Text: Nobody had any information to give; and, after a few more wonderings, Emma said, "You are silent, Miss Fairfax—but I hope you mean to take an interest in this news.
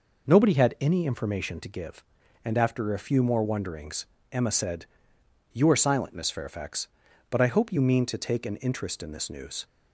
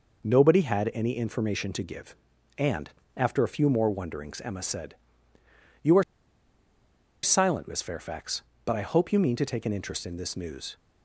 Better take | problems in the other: first | pauses between "are" and "silent"; at 6.0 s; 1.1 s long

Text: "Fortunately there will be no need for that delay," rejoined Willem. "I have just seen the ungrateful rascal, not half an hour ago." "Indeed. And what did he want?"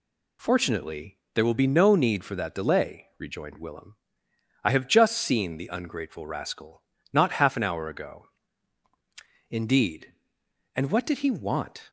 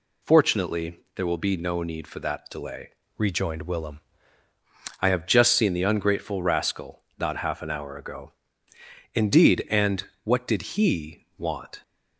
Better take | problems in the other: first | pauses between "Fortunately" and "there"; slight; at 0.9 s; 0.16 s long; slight in the first // changes voice from "rejoined" to "Willem"; from 3.1 to 4.0 s; 0.9 s long // pauses between "And" and "what"; slight; at 10.0 s; 0.20 s long

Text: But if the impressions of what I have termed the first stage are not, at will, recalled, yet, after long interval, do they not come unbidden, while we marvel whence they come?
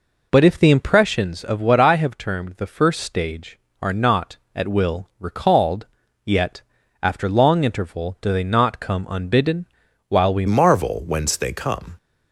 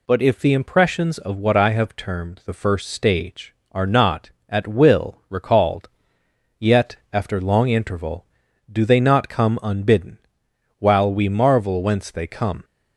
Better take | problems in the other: second | changes voice at "marvel"; from 10.4 s on; 1.5 s long

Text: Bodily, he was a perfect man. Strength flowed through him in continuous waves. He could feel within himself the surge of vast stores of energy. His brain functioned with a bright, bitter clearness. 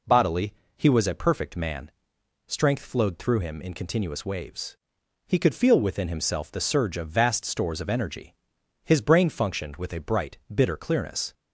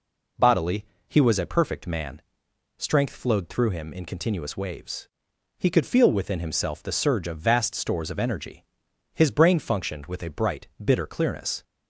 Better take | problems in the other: neither | none

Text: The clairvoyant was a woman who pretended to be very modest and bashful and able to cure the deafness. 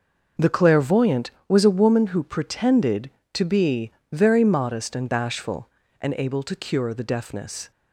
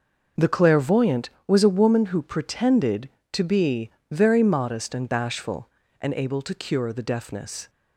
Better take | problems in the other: neither | pauses between "be" and "very"; slight; the same in both

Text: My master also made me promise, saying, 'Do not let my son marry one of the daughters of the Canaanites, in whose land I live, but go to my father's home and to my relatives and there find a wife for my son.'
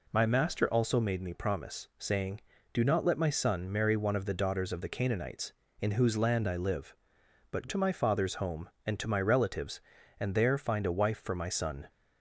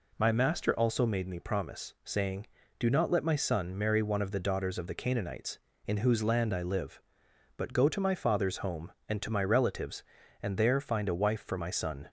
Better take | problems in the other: second | skips "go"; at 7.6 s

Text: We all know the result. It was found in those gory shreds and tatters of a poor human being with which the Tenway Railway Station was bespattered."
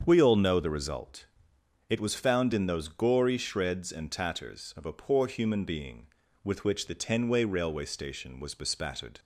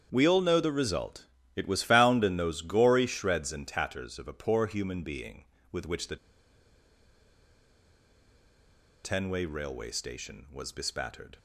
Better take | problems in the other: first | starts louder than the rest; strong; until 1.1 s; 8 dB; strong in the first // pauses between "the" and "Tenway"; strong; at 6.1 s; 2.8 s long

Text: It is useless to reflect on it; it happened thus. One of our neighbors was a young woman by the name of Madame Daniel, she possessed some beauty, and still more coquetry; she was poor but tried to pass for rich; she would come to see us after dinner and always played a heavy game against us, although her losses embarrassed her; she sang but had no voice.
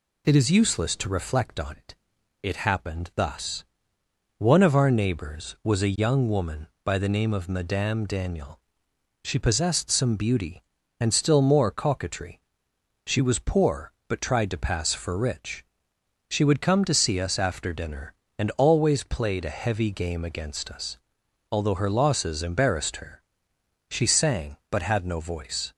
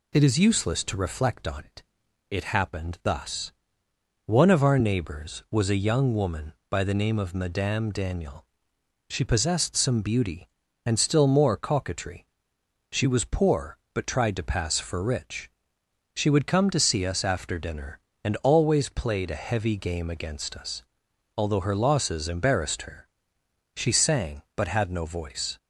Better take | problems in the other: neither | none

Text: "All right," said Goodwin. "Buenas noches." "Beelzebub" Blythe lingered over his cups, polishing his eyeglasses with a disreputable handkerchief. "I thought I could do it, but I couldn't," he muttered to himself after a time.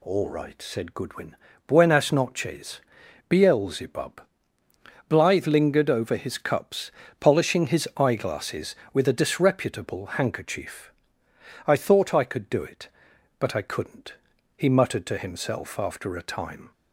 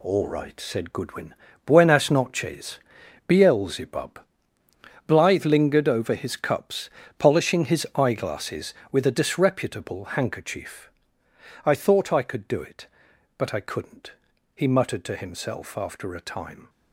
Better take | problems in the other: first | gets quieter; strong; throughout; 7.5 dB // pauses between "Beelzebub" and "Blythe"; noticeable; at 4.1 s; 0.88 s long; noticeable in the first

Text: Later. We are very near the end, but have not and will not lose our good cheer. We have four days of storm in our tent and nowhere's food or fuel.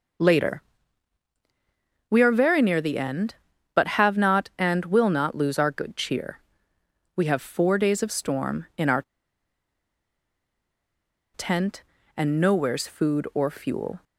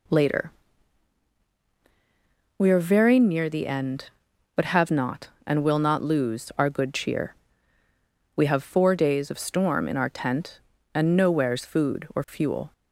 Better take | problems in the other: second | pauses between "our" and "tent"; strong; at 9.0 s; 2.3 s long

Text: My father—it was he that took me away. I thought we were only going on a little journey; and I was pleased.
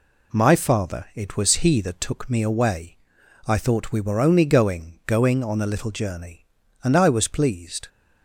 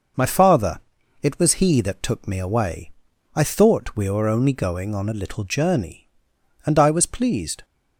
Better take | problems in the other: second | says "going" twice; at 5.0 s

